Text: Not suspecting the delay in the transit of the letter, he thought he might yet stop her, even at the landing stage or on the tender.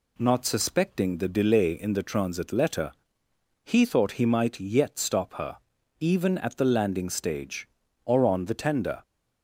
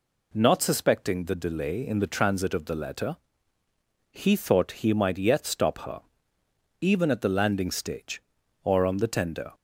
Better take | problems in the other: second | skips "of the"; at 2.4 s

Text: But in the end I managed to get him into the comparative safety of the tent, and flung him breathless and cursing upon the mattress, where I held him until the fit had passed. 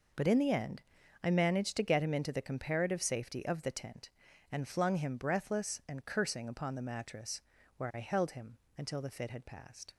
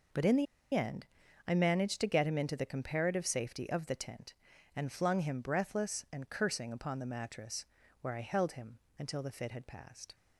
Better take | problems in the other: first | pauses between "the" and "end"; slight; at 0.4 s; 0.29 s long // pauses between "end" and "I"; at 1.0 s; 0.40 s long; also in the first // pauses between "him" and "until"; slight; at 8.7 s; 0.18 s long; slight in the first

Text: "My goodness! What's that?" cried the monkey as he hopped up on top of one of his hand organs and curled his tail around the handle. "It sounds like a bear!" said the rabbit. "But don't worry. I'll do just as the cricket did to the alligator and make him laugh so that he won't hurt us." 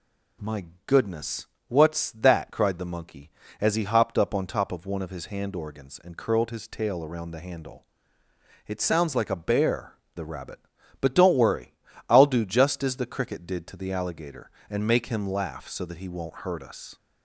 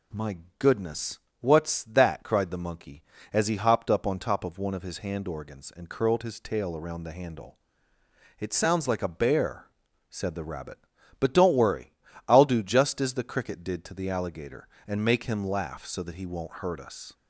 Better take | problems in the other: second | pauses between "My" and "goodness"; slight; at 0.6 s; 0.20 s long; slight in the second // skips "said"; at 10.0 s

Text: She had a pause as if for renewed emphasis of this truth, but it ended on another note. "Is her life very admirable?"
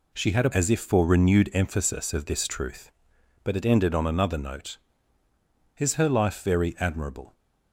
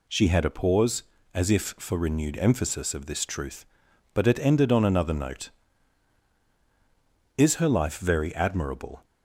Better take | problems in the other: second | skips "pause"; at 0.5 s

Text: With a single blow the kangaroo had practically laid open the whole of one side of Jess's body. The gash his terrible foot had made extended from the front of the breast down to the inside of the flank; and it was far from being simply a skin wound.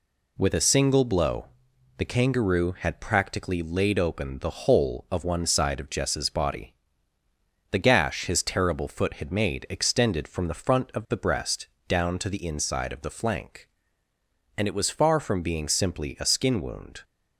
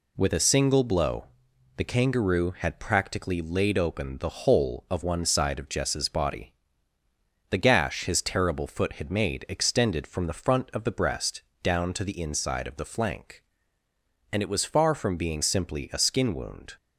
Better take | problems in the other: neither | pauses between "blow" and "the"; noticeable; the same in both // pauses between "breast" and "down"; slight; the same in both

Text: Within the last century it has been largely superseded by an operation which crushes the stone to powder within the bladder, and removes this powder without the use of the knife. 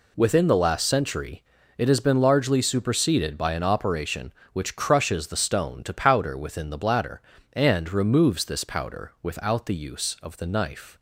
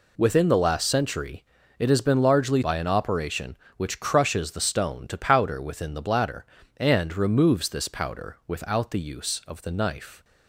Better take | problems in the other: first | pauses between "century" and "it"; slight; at 1.4 s; 0.34 s long; slight in the first // skips "superseded"; at 2.6 s

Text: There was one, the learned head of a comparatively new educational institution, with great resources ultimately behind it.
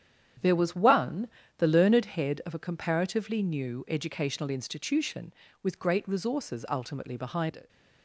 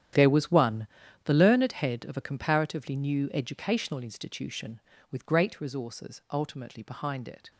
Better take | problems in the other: first | gets quieter; strong; throughout; 14.5 dB // starts louder than the rest; strong; until 1.5 s; 10 dB; strong in the first

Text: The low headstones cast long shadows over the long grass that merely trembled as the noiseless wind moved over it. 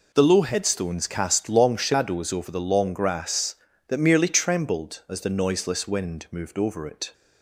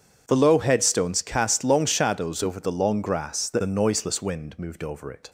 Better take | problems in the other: first | starts louder than the rest; strong; until 1.2 s; 7.5 dB // skips "merely trembled as"; at 3.6 s

